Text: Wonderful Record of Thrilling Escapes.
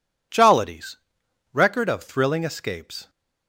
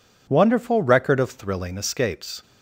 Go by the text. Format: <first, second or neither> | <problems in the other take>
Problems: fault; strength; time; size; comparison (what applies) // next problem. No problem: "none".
second | says "Jollities" for "Wonderful"; at 0.3 s